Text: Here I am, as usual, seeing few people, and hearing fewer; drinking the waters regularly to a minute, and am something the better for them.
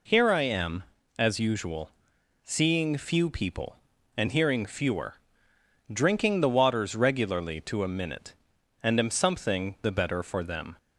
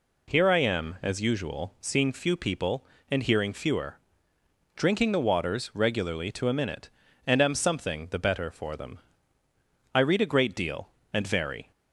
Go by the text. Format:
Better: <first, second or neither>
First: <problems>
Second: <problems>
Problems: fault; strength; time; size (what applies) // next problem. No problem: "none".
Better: first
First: none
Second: goes on to say "I read a great deal and vary"; strong; from 9.9 s on; 1.7 s long